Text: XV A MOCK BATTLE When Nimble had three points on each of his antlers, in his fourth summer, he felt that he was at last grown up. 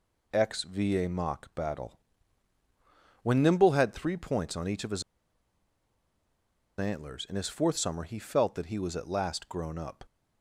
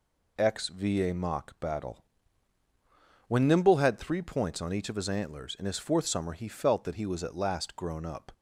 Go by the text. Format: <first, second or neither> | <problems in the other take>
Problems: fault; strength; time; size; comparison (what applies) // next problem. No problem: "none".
second | pauses between "BATTLE" and "When"; strong; at 1.9 s; 1.2 s long; strong in the second // pauses between "his" and "antlers"; strong; at 5.0 s; 1.7 s long